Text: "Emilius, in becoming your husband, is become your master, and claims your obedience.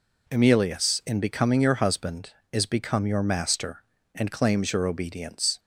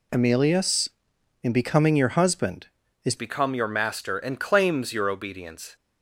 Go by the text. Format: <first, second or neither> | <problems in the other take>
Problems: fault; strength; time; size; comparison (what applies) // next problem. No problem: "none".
first | changes voice at "become"; from 3.1 s on; 2.6 s long